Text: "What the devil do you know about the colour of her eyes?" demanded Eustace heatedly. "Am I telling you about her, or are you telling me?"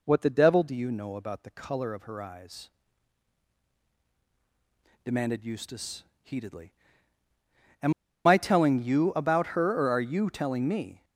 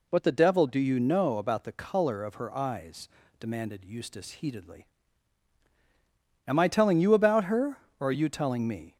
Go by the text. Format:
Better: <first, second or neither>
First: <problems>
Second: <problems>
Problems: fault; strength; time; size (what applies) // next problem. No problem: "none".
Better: second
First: pauses between "Eustace" and "heatedly"; slight; at 6.0 s; 0.20 s long // pauses between "Am" and "I"; slight; at 7.9 s; 0.33 s long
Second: none